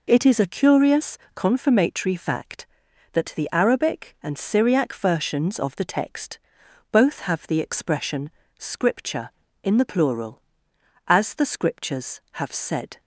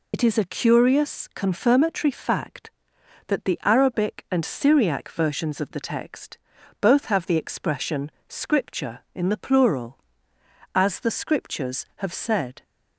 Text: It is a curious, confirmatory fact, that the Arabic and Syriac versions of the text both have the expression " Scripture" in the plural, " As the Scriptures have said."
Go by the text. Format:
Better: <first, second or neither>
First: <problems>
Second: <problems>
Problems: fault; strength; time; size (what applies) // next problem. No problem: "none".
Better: first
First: pauses between "text" and "both"; noticeable; at 6.3 s; 0.52 s long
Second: loses the start of "It"; at 0.1 s; 75 ms // pauses between "text" and "both"; at 6.3 s; 0.42 s long